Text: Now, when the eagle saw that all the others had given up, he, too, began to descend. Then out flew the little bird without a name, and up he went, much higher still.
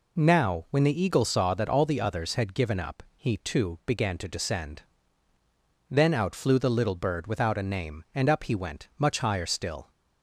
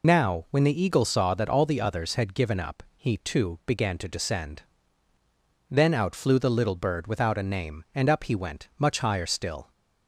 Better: first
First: none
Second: loses the start of "Now"; at 0.0 s; 85 ms

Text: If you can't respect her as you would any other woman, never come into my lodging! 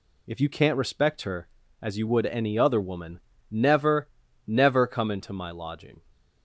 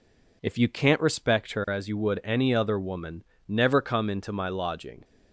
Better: second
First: says "never" twice; at 4.4 s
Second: none

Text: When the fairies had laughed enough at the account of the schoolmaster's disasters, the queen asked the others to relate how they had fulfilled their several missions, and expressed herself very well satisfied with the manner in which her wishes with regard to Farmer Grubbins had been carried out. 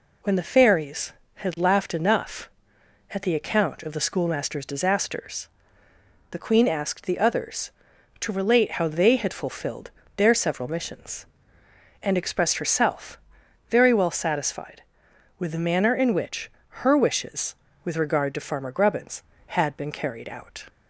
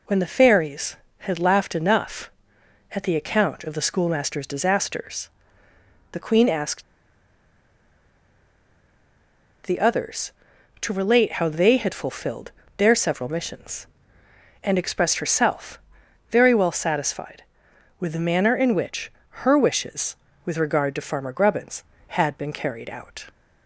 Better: first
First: pauses between "fulfilled" and "their"; slight; at 9.9 s; 0.26 s long // pauses between "herself" and "very"; noticeable; at 13.1 s; 0.50 s long // pauses between "which" and "her"; slight; at 16.4 s; 0.32 s long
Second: pauses between "asked" and "the"; strong; at 6.8 s; 2.8 s long // pauses between "fulfilled" and "their"; slight; at 12.5 s; 0.26 s long // pauses between "herself" and "very"; noticeable; at 15.7 s; 0.50 s long // pauses between "which" and "her"; slight; at 19.0 s; 0.32 s long

